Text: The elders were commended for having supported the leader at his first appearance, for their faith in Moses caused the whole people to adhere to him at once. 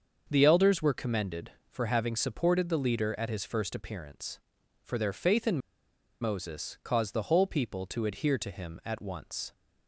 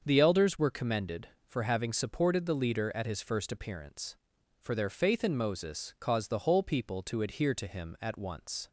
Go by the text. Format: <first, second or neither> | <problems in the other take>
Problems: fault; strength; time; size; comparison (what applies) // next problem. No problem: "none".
second | starts louder than the rest; until 1.3 s; 6.5 dB; also in the second // pauses between "in" and "Moses"; noticeable; at 5.5 s; 0.63 s long